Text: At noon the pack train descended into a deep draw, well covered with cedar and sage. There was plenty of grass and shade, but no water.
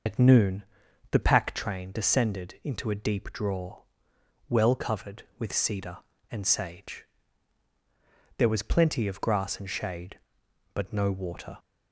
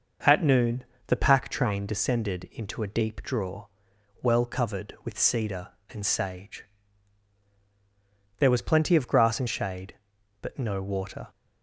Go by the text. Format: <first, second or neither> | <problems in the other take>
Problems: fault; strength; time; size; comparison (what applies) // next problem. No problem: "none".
second | loses the start of "At"; at 0.0 s; 65 ms // pauses between "noon" and "the"; noticeable; at 0.6 s; 0.46 s long; slight in the second